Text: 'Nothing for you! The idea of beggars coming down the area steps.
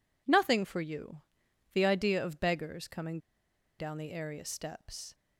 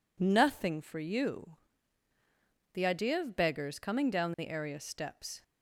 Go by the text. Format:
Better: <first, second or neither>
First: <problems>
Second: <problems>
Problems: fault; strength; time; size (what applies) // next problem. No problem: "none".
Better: second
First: pauses between "coming" and "down"; noticeable; at 3.1 s; 0.61 s long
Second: none